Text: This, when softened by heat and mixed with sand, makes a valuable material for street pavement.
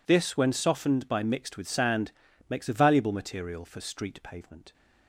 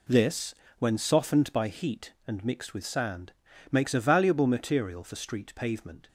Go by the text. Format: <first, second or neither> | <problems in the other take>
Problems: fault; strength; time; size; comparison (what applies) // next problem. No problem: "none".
second | skips "heat and"; at 1.2 s